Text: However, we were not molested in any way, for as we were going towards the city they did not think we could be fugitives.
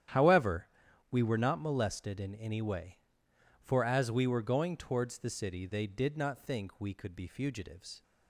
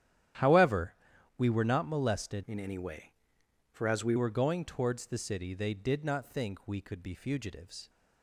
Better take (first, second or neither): first